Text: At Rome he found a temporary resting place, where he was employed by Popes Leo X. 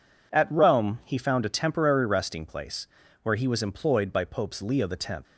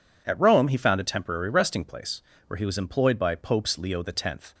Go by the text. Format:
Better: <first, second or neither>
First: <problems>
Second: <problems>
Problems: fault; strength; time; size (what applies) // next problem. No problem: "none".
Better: neither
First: none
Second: none